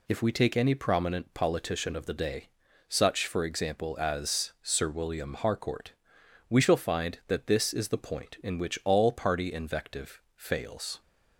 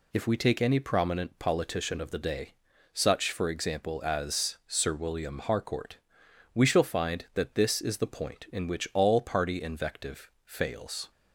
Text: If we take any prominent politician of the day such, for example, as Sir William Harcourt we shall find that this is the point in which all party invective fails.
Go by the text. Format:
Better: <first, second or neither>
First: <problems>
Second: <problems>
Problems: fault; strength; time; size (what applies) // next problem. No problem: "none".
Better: neither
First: pauses between "day" and "such"; at 2.4 s; 0.40 s long // pauses between "Harcourt" and "we"; noticeable; at 5.9 s; 0.56 s long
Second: pauses between "day" and "such"; at 2.5 s; 0.40 s long // pauses between "Harcourt" and "we"; noticeable; at 5.9 s; 0.56 s long